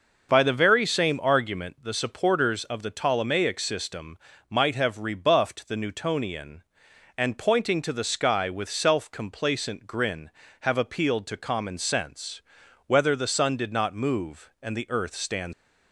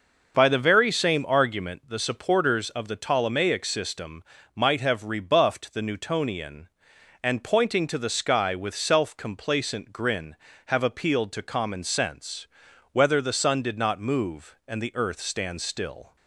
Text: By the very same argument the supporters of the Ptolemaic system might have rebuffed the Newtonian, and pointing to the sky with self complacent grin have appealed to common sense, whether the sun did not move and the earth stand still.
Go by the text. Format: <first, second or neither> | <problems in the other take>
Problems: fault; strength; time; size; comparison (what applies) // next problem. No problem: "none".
second | starts louder than the rest; until 1.3 s; 6 dB; also in the second // pauses between "system" and "might"; slight; at 4.1 s; 0.32 s long; slight in the second // stops before "still"; at 15.5 s